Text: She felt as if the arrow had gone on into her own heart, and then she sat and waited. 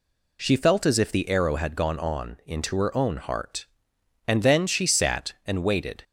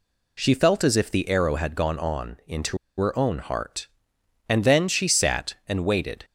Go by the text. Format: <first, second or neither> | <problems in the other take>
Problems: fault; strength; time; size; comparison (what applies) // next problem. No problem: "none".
first | pauses between "into" and "her"; slight; at 2.7 s; 0.21 s long